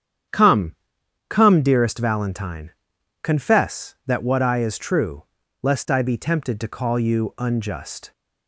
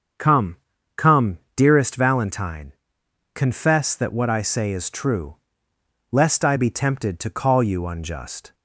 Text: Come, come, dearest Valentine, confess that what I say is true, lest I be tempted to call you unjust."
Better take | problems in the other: second | starts louder than the rest; strong; until 1.8 s; 9.5 dB; also in the second // skips "say"; at 4.5 s

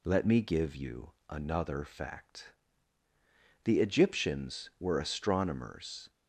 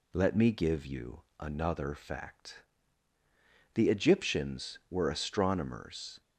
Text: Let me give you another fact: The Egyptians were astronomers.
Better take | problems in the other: neither | none

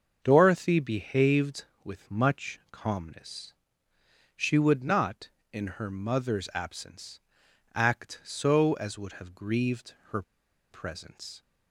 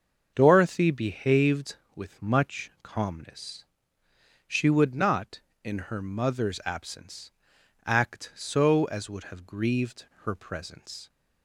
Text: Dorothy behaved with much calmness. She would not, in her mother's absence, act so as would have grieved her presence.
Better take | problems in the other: second | starts louder than the rest; until 1.2 s; 6.5 dB; also in the second // pauses between "grieved" and "her"; slight; at 9.9 s; 0.16 s long; slight in the second // pauses between "her" and "presence"; noticeable; at 10.2 s; 0.48 s long

